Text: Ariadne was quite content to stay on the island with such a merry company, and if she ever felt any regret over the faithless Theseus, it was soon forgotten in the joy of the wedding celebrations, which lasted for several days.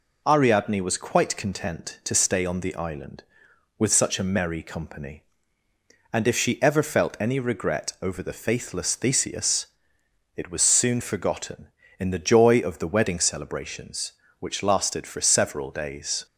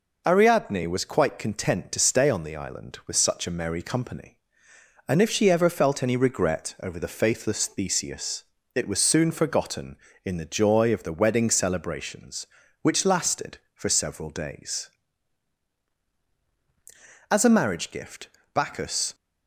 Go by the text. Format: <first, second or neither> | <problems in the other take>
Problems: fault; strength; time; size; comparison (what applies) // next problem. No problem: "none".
first | goes on to say "As a marriage gift Bacchus"; strong; from 17.3 s on; 1.8 s long